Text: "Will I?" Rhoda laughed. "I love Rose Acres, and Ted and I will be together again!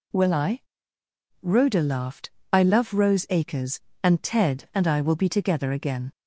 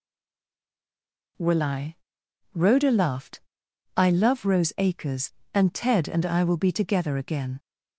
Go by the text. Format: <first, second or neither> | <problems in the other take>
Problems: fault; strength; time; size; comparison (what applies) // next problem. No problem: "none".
first | stays silent before the first word; noticeable; until 1.3 s; 1.3 s long